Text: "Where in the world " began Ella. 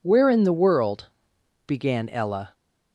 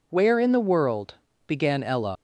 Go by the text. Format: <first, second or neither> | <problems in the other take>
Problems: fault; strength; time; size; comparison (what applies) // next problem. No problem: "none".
first | leaves "Ella" unfinished; at 2.1 s; 120 ms